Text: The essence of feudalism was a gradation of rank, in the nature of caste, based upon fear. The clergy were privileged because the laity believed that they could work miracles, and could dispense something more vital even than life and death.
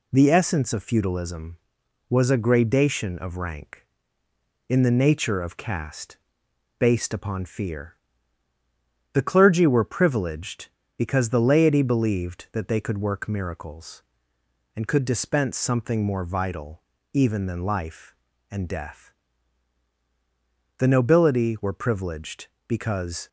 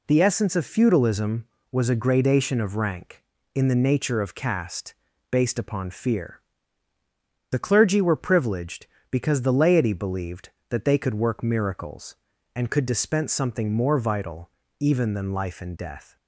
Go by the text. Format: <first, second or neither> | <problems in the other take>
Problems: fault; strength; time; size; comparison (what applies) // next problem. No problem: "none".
second | pauses between "vital" and "even"; slight; at 16.8 s; 0.32 s long; slight in the second // goes on to say "The nobility were privileged because"; strong; from 20.7 s on; 2.4 s long